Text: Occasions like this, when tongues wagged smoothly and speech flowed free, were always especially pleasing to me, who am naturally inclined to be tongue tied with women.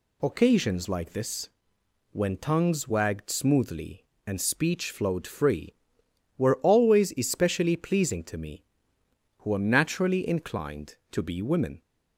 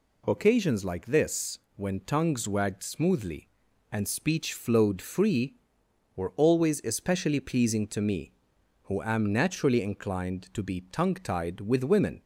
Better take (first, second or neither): second